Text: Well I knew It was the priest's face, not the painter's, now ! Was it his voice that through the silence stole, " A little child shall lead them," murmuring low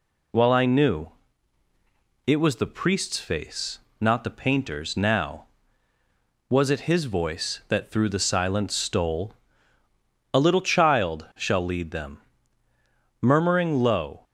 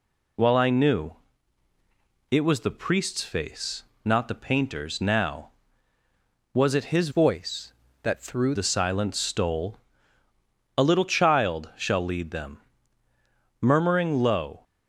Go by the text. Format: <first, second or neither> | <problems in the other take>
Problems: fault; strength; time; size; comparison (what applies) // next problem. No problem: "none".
first | pauses between "knew" and "It"; at 1.1 s; 1.1 s long; also in the first // changes voice from "voice" to "through"; from 7.1 to 8.5 s; 1.4 s long